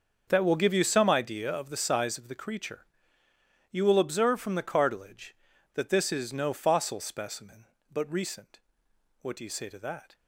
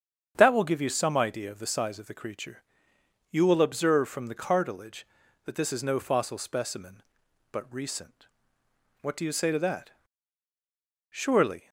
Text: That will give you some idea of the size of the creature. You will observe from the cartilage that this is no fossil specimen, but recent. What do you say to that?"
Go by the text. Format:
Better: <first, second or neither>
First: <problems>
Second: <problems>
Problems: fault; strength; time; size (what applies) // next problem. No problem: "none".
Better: first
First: starts louder than the rest; until 1.3 s; 6.5 dB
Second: starts louder than the rest; strong; until 1.3 s; 8 dB // goes on to say "Surely"; from 11.1 s on; 0.58 s long